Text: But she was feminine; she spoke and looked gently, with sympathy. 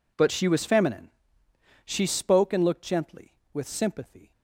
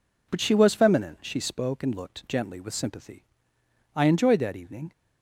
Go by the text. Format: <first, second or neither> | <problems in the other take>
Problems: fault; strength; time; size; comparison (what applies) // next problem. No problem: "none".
first | goes on to say "I enjoyed that evening"; noticeable; from 3.9 s on; 0.96 s long